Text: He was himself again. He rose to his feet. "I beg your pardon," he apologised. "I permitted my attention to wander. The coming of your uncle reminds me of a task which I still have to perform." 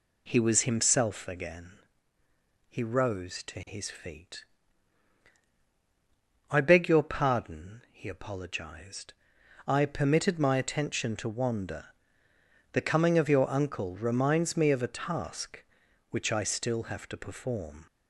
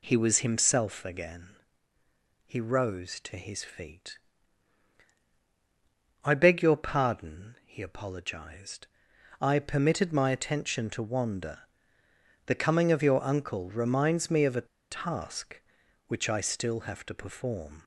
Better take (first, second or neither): first